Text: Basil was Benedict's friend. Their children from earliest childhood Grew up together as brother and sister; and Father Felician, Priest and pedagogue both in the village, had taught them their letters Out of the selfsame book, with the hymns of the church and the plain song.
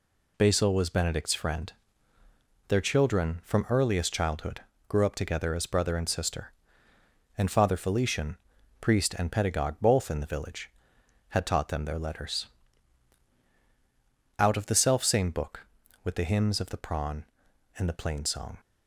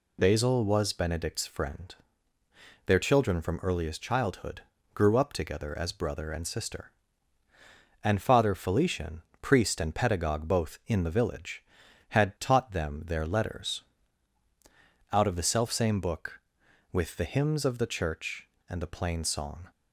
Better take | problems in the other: second | pauses between "childhood" and "Grew"; slight; at 4.6 s; 0.26 s long; slight in the second // pauses between "letters" and "Out"; strong; at 12.4 s; 1.9 s long; strong in the second // says "prawn" for "church"; at 16.7 s

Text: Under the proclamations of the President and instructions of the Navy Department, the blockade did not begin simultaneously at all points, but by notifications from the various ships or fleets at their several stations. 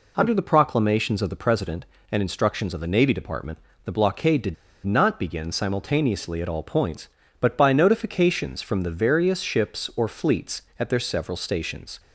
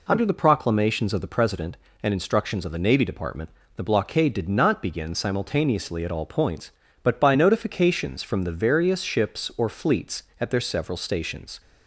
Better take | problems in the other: second | pauses between "did" and "not"; slight; at 4.5 s; 0.30 s long

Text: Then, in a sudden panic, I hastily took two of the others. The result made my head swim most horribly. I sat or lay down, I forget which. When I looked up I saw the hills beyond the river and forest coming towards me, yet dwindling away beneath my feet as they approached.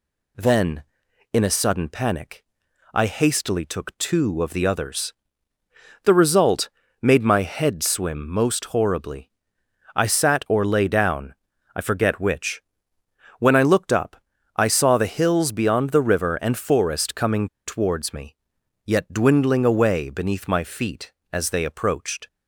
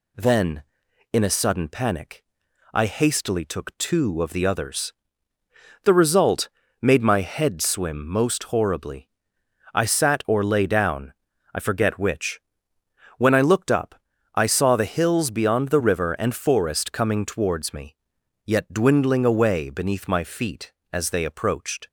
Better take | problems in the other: second | pauses between "result" and "made"; slight; at 6.6 s; 0.34 s long; slight in the second // pauses between "up" and "I"; at 14.1 s; 0.40 s long; also in the second // pauses between "coming" and "towards"; slight; at 17.4 s; 0.20 s long

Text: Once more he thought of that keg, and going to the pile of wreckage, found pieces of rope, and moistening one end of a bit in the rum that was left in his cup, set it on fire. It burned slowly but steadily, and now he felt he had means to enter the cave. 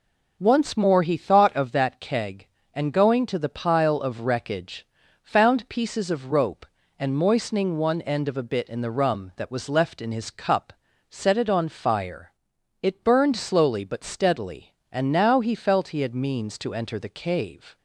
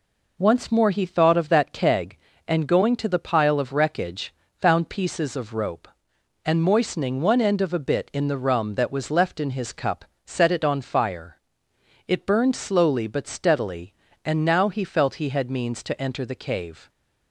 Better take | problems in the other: neither | none

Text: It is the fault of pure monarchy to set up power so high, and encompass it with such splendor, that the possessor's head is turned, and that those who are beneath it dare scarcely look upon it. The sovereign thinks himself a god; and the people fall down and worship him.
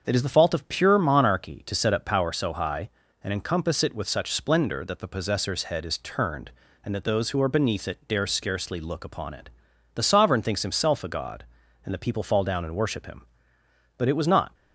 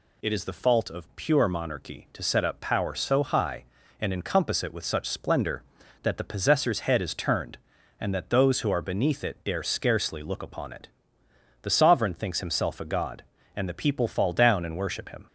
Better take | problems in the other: second | starts louder than the rest; until 1.0 s; 6.5 dB // goes on to say "But it was not"; from 13.9 s on; 0.56 s long

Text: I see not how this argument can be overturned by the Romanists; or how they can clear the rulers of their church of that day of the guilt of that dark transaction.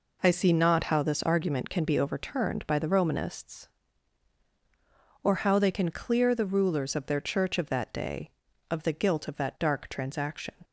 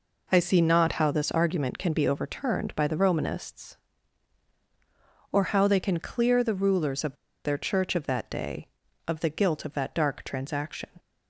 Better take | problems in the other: first | pauses between "of" and "their"; slight; at 7.1 s; 0.29 s long

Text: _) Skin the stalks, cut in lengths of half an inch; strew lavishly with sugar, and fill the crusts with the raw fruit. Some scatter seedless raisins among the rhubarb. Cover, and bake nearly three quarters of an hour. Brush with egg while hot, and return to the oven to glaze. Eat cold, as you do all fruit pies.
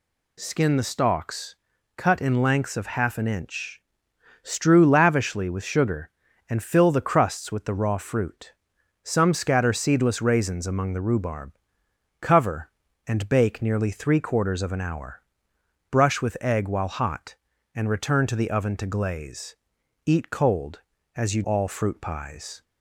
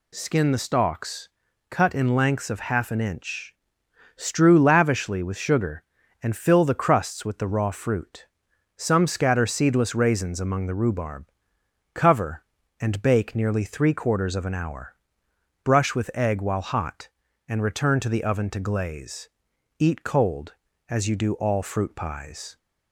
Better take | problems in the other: second | skips "do"; at 21.4 s

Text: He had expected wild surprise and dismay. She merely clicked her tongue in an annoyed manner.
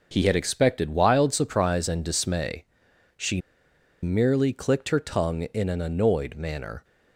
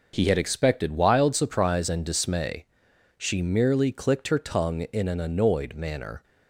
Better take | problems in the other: second | pauses between "She" and "merely"; noticeable; at 3.4 s; 0.62 s long

